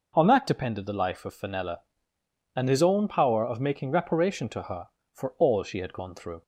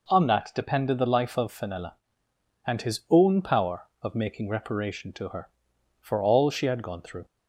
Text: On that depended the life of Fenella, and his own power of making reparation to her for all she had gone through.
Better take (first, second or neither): neither